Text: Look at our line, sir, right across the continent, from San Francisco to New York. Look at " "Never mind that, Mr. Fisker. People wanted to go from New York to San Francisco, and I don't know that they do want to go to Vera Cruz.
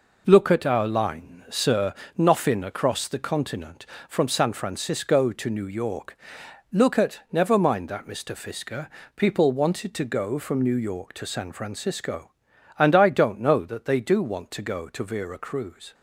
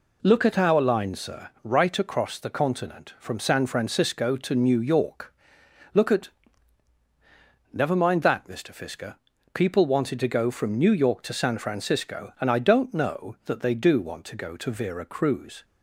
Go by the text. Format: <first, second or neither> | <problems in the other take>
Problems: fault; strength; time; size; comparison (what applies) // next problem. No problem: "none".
second | says "noffin" for "right"; at 2.1 s